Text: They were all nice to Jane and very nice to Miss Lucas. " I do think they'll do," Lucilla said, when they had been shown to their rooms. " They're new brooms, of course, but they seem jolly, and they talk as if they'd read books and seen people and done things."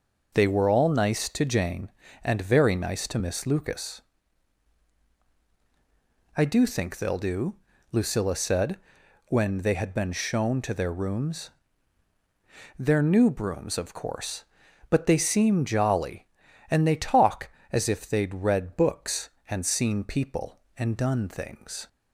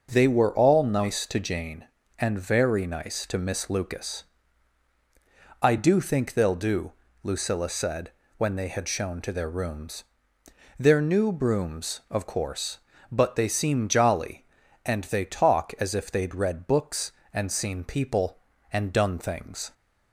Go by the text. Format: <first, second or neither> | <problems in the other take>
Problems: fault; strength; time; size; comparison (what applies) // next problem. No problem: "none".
first | starts louder than the rest; strong; until 1.1 s; 7.5 dB; also in the first // skips "been"; at 8.8 s